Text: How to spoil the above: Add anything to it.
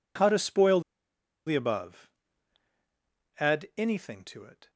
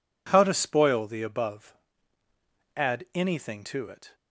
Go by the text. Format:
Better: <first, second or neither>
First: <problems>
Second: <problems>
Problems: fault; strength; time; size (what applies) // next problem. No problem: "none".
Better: second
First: pauses between "spoil" and "the"; noticeable; at 0.8 s; 0.66 s long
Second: none